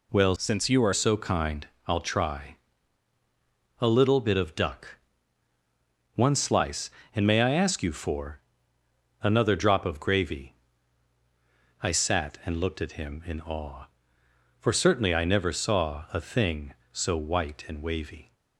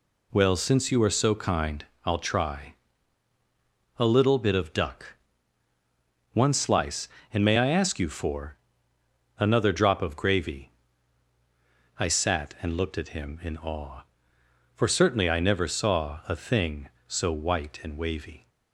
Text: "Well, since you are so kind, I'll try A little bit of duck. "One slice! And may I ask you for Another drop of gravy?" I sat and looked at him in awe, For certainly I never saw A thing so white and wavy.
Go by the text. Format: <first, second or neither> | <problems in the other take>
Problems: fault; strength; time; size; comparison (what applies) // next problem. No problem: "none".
second | changes voice from "since" to "are"; from 0.3 to 0.9 s; 0.6 s long // pauses between "try" and "A"; at 2.5 s; 1.2 s long; also in the second // pauses between "for" and "Another"; noticeable; at 8.3 s; 0.84 s long; noticeable in the second